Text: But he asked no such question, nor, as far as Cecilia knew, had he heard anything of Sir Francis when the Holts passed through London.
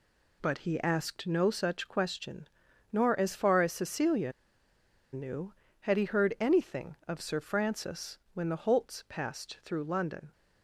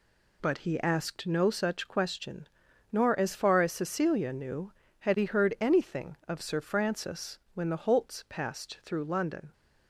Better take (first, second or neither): second